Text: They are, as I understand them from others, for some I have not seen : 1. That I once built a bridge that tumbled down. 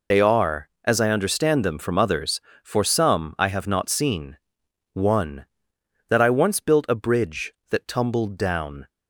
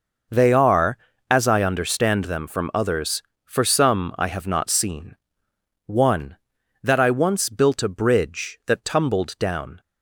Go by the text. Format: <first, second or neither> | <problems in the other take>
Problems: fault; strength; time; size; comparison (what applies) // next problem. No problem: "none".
second | loses the start of "They"; at 0.1 s; 60 ms